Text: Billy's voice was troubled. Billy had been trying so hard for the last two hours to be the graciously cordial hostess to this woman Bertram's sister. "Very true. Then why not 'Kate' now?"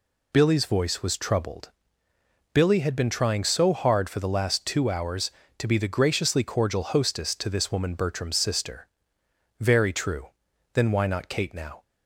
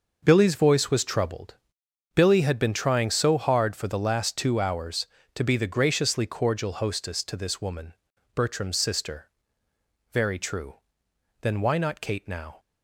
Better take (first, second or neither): first